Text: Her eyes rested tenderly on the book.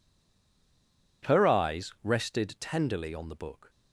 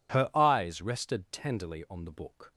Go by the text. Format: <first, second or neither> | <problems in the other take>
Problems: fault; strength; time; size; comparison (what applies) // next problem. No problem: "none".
second | stays silent before the first word; noticeable; until 1.2 s; 1.2 s long